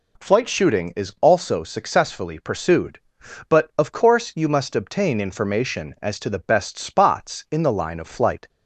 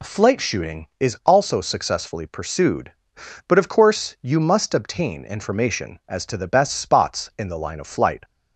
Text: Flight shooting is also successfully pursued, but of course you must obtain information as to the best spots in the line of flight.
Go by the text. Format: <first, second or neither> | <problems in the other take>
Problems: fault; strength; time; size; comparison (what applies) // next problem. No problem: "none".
neither | none